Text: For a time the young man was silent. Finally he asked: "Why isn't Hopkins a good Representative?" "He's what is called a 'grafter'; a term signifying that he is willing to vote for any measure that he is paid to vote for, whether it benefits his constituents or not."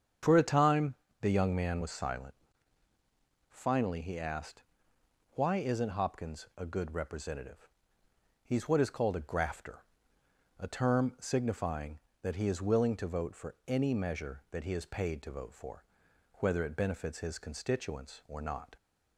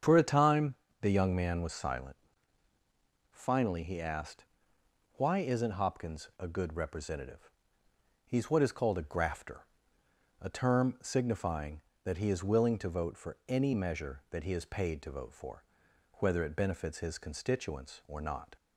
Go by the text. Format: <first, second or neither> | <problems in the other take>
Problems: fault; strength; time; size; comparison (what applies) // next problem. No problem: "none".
neither | starts louder than the rest; strong; the same in both // pauses between "time" and "the"; slight; the same in both